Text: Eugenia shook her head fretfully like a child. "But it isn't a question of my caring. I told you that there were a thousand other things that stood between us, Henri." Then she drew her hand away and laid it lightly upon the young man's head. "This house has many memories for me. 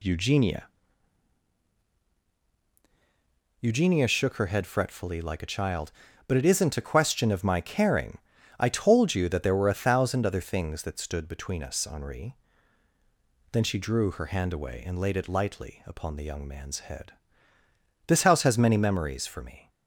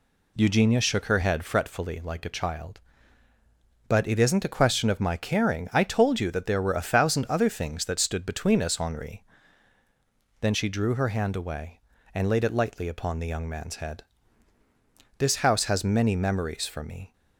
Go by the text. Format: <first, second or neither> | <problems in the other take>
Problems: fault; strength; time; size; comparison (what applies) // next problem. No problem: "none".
second | says "Eugenia" twice; at 3.6 s